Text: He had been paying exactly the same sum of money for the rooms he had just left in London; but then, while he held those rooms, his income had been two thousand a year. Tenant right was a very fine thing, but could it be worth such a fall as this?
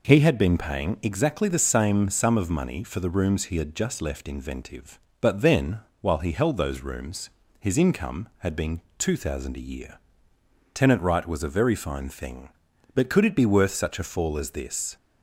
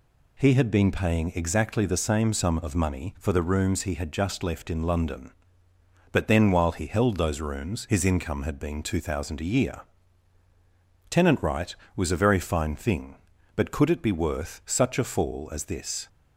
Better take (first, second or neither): second